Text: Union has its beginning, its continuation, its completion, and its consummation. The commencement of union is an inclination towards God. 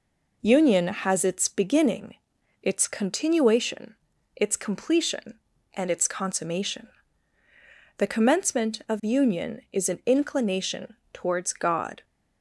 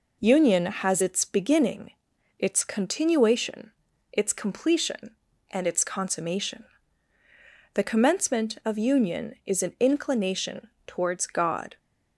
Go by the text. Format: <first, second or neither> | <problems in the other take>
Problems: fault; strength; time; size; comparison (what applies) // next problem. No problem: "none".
neither | pauses between "inclination" and "towards"; slight; the same in both